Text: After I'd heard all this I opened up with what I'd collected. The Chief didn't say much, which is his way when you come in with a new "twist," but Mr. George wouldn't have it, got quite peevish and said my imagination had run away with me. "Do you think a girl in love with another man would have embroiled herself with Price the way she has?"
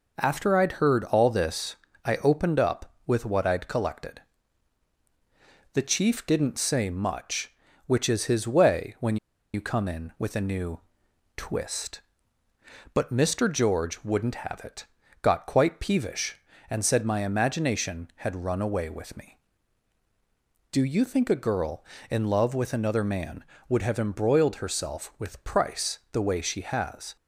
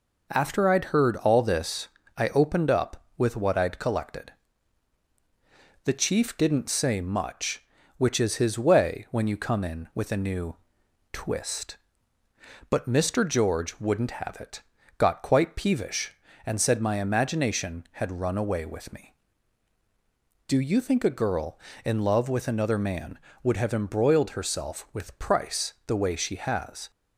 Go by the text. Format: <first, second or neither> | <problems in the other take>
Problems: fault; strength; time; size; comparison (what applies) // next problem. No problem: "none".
second | pauses between "this" and "I"; slight; at 1.7 s; 0.28 s long; slight in the second // pauses between "when" and "you"; at 9.1 s; 0.37 s long // pauses between "new" and "twist"; noticeable; at 10.7 s; 0.56 s long; noticeable in the second // pauses between "Price" and "the"; slight; at 25.9 s; 0.16 s long; slight in the second